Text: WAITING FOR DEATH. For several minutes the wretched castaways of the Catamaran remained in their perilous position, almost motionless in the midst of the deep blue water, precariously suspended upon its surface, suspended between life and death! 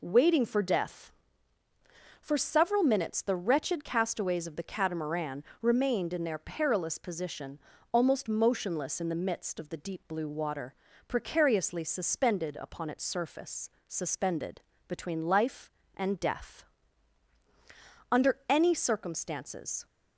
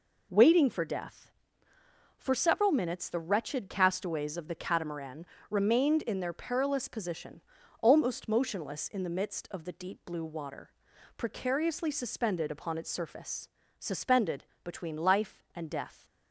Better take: second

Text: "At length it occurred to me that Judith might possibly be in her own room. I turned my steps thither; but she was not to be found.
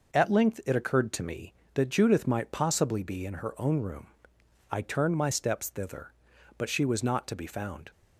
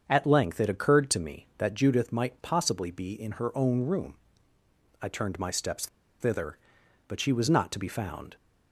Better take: first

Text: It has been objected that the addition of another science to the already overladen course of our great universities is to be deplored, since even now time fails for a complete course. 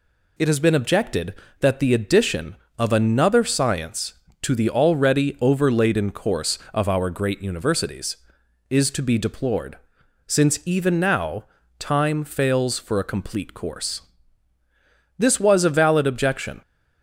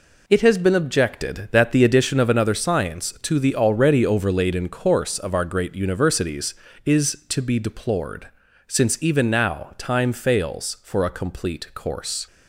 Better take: second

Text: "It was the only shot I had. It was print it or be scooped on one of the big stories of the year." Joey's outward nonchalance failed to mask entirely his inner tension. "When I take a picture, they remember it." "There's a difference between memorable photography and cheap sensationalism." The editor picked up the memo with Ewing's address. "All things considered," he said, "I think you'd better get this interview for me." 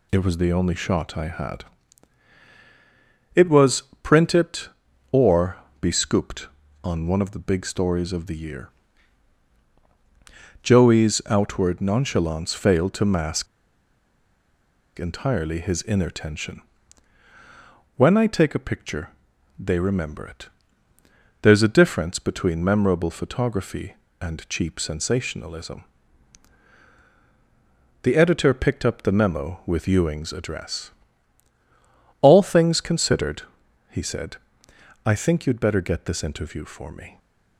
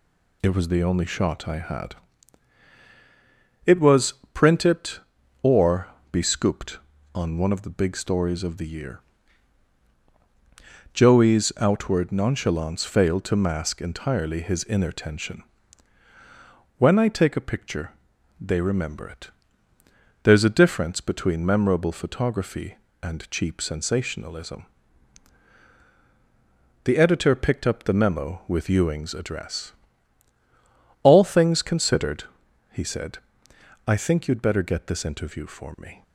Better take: second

